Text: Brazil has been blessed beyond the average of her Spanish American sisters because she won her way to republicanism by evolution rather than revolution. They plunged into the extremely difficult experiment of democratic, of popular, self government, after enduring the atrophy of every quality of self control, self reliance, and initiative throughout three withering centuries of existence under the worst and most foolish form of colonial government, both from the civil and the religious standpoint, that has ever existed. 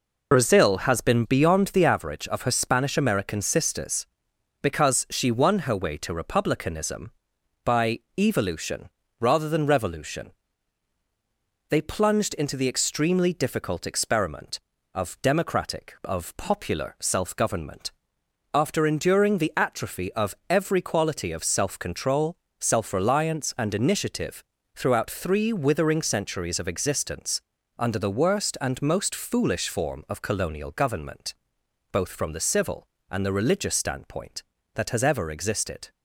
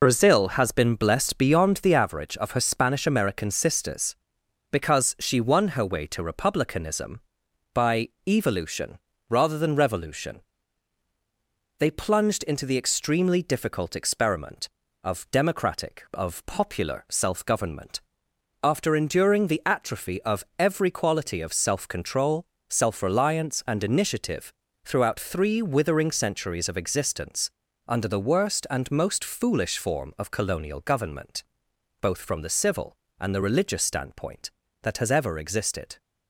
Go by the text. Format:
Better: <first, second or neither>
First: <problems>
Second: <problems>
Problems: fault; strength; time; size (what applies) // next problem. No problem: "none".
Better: second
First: skips "blessed"; at 1.2 s // pauses between "by" and "evolution"; slight; at 7.9 s; 0.18 s long // pauses between "evolution" and "rather"; slight; at 8.8 s; 0.30 s long // pauses between "of" and "every"; slight; at 20.3 s; 0.16 s long // pauses between "initiative" and "throughout"; slight; at 24.4 s; 0.32 s long // pauses between "existence" and "under"; slight; at 27.4 s; 0.34 s long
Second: pauses between "by" and "evolution"; slight; at 8.0 s; 0.18 s long // pauses between "evolution" and "rather"; slight; at 8.9 s; 0.30 s long // pauses between "of" and "every"; slight; at 20.4 s; 0.16 s long // pauses between "initiative" and "throughout"; slight; at 24.5 s; 0.32 s long // pauses between "existence" and "under"; slight; at 27.5 s; 0.34 s long